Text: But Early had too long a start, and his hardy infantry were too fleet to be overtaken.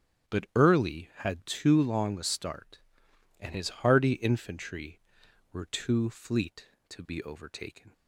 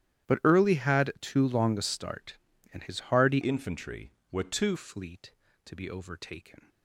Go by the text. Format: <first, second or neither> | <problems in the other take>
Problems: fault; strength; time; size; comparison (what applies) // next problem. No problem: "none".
first | starts louder than the rest; strong; until 1.3 s; 12 dB; strong in the first // changes voice from "infantry" to "too"; from 3.4 to 4.7 s; 1.3 s long